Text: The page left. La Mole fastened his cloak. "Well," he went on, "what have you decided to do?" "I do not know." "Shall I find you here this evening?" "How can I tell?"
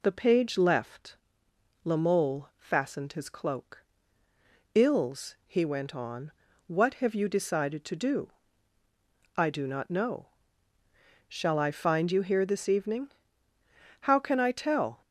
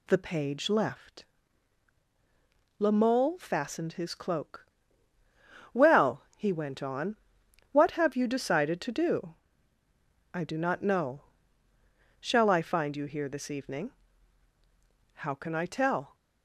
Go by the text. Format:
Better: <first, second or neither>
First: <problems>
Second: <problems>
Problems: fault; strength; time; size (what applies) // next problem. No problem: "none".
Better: second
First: says "Ills" for "Well"; at 4.7 s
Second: none